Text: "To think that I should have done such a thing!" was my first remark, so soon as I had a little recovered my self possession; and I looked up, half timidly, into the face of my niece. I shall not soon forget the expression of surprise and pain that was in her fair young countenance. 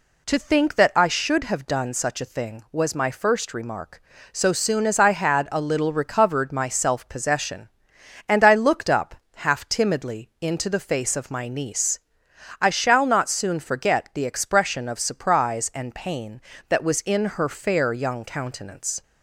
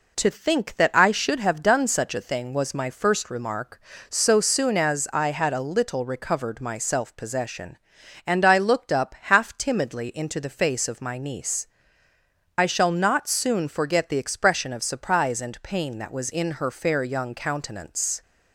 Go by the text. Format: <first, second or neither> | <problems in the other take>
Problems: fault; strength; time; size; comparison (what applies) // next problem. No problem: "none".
neither | none